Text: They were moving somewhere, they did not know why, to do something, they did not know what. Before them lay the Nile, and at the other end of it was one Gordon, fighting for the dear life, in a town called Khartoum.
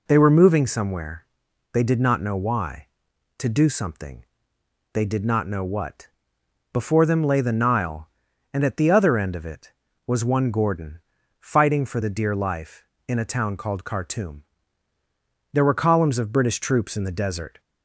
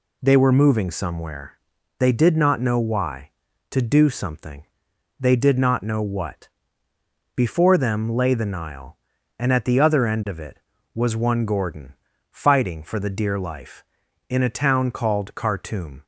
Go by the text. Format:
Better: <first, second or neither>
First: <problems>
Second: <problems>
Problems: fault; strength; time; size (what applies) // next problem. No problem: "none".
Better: second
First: goes on to say "There were columns of British troops in the desert"; strong; from 15.5 s on; 2.0 s long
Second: none